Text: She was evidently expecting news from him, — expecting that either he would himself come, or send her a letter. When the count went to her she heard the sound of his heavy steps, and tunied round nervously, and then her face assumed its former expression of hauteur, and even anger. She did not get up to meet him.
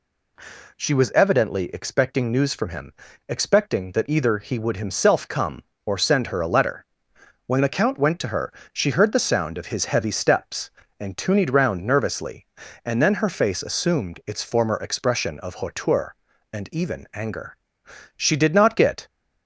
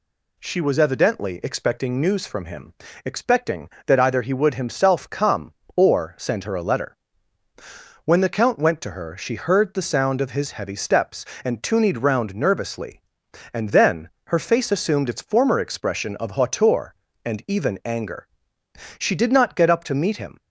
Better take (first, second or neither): second